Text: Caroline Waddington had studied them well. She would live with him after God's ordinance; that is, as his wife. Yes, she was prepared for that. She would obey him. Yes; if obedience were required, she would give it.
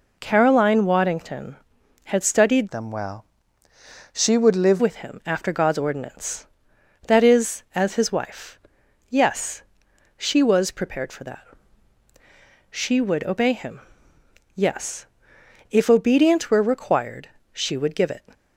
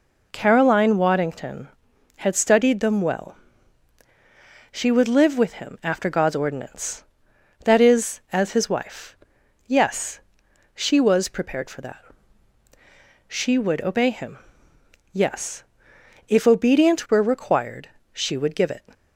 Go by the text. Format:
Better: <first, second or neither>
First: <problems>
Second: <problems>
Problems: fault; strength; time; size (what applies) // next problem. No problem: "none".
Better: second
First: changes voice from "them" to "live"; from 2.6 to 4.8 s; 2.2 s long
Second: none